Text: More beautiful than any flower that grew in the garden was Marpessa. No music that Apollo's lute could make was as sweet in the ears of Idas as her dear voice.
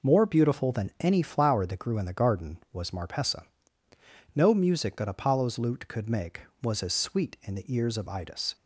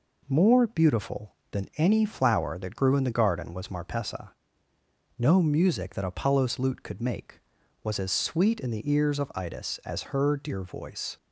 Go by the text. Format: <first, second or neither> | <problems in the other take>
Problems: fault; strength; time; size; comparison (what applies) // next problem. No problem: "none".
second | stops before "as her dear voice"; at 8.5 s